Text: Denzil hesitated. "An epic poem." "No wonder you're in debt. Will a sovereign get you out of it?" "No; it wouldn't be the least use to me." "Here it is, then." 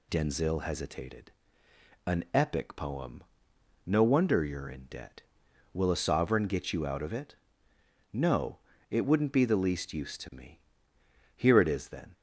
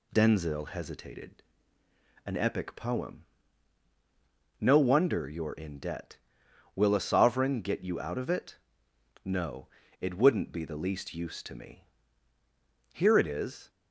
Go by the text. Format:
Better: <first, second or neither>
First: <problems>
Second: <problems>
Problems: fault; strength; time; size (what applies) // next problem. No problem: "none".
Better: first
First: none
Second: stops before "then"; at 13.6 s